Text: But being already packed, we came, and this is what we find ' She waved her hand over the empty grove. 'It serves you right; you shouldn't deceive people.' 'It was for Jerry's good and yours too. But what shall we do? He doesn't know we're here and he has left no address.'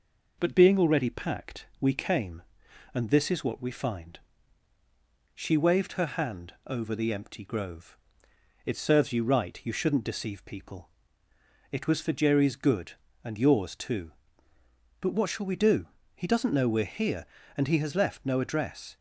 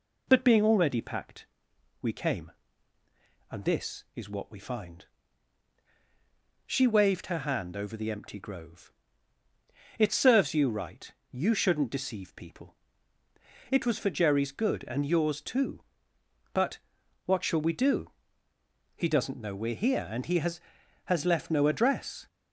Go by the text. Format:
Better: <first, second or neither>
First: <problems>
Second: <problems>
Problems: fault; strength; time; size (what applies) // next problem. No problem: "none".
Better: first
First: none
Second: pauses between "But" and "what"; noticeable; at 16.7 s; 0.48 s long // says "has" twice; at 21.0 s